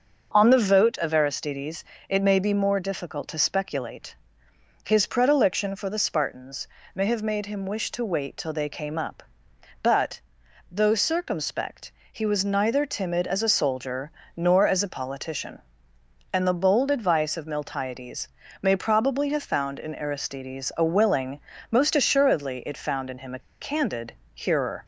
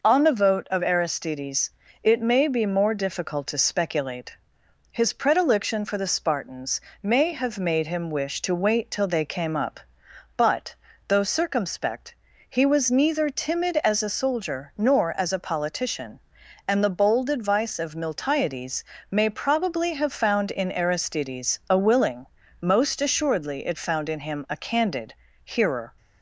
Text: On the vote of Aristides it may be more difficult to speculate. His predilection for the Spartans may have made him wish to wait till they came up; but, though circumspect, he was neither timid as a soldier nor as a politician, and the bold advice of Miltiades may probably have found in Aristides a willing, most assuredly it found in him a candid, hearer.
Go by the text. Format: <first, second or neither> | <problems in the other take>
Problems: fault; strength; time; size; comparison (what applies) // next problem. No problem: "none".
second | starts louder than the rest; until 1.3 s; 6 dB // pauses between "Aristides" and "it"; slight; at 1.8 s; 0.24 s long; slight in the second // pauses between "Spartans" and "may"; slight; at 6.6 s; 0.28 s long; slight in the second // pauses between "soldier" and "nor"; slight; at 14.1 s; 0.24 s long // pauses between "Miltiades" and "may"; slight; at 18.2 s; 0.34 s long; slight in the second // pauses between "a" and "candid"; slight; at 23.4 s; 0.23 s long